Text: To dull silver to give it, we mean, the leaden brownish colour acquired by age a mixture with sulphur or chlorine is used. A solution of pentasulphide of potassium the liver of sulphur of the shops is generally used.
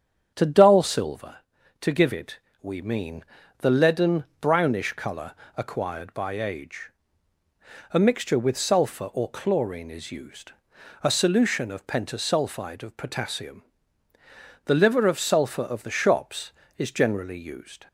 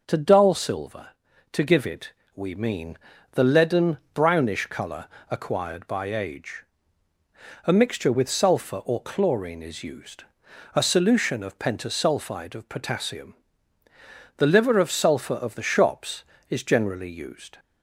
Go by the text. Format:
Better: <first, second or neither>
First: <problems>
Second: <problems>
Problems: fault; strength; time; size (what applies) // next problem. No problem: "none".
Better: second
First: starts louder than the rest; strong; until 1.3 s; 8 dB // pauses between "leaden" and "brownish"; slight; at 4.2 s; 0.16 s long // pauses between "colour" and "acquired"; slight; at 5.3 s; 0.24 s long // pauses between "age" and "a"; at 6.9 s; 1.0 s long // pauses between "potassium" and "the"; at 13.6 s; 1.0 s long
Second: pauses between "leaden" and "brownish"; slight; at 3.9 s; 0.16 s long // pauses between "colour" and "acquired"; slight; at 5.0 s; 0.24 s long // pauses between "age" and "a"; at 6.6 s; 1.0 s long // pauses between "potassium" and "the"; at 13.3 s; 1.0 s long